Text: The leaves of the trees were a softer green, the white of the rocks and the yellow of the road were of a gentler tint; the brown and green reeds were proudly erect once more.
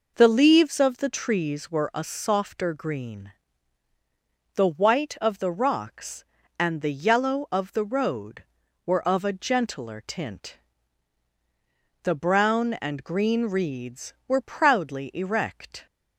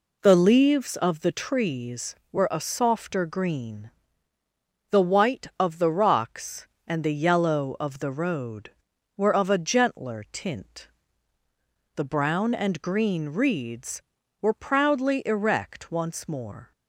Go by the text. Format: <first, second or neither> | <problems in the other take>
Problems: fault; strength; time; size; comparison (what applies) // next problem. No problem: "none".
second | stops before "once more"; at 15.8 s